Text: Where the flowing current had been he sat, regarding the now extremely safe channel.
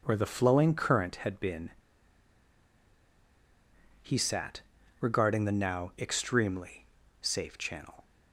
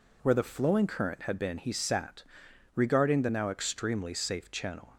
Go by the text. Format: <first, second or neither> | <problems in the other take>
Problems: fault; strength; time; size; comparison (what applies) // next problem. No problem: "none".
second | pauses between "been" and "he"; strong; at 1.6 s; 2.3 s long // pauses between "extremely" and "safe"; slight; at 6.8 s; 0.36 s long